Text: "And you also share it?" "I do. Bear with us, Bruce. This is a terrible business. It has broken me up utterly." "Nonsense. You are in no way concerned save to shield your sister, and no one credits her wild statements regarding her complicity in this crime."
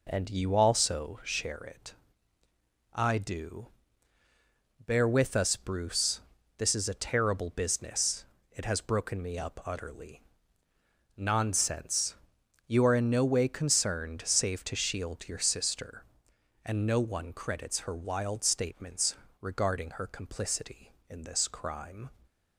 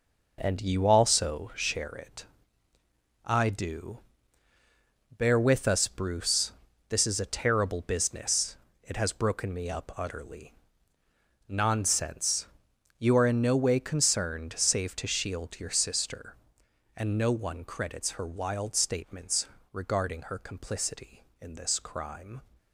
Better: first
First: pauses between "statements" and "regarding"; slight; at 19.1 s; 0.26 s long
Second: gets quieter; strong; throughout; 7.5 dB // pauses between "statements" and "regarding"; slight; at 19.4 s; 0.26 s long

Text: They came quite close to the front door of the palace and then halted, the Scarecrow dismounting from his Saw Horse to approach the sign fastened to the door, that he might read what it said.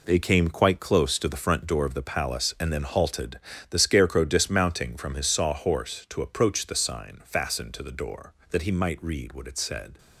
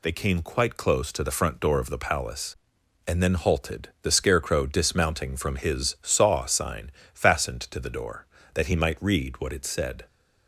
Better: first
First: none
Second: skips "Horse to approach the"; at 6.4 s // pauses between "sign" and "fastened"; slight; at 6.8 s; 0.24 s long

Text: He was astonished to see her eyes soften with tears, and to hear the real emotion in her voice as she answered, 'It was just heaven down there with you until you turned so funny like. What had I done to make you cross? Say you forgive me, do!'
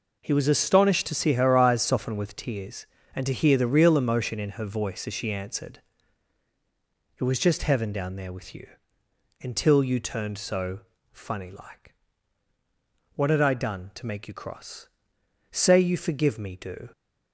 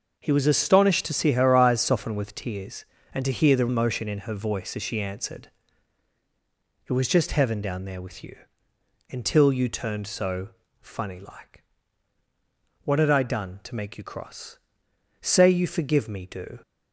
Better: first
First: pauses between "you" and "until"; noticeable; at 8.6 s; 0.74 s long // pauses between "so" and "funny"; slight; at 10.7 s; 0.32 s long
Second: starts louder than the rest; noticeable; until 1.2 s; 6 dB // skips "real"; at 3.6 s // pauses between "you" and "until"; noticeable; at 8.3 s; 0.74 s long // pauses between "so" and "funny"; slight; at 10.4 s; 0.32 s long

